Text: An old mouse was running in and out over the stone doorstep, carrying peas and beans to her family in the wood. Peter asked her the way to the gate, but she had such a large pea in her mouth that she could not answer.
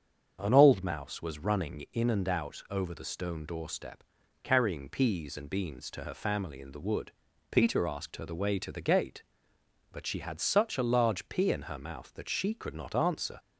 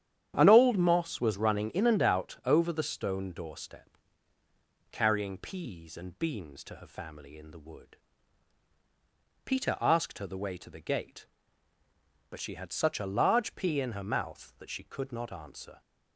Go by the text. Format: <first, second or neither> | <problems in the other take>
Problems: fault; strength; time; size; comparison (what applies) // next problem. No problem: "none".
first | starts louder than the rest; strong; until 1.3 s; 9.5 dB; also in the first // says "moss" for "mouse"; at 0.7 s